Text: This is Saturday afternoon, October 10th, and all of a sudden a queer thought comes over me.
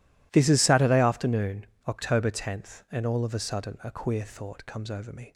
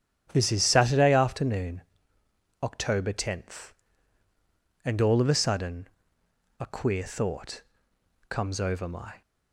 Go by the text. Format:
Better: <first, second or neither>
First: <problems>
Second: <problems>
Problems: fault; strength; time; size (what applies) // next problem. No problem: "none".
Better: first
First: none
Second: starts louder than the rest; strong; until 1.3 s; 9.5 dB // pauses between "sudden" and "a"; noticeable; at 5.8 s; 0.72 s long // pauses between "thought" and "comes"; noticeable; at 7.6 s; 0.68 s long // says "my" for "me"; at 8.8 s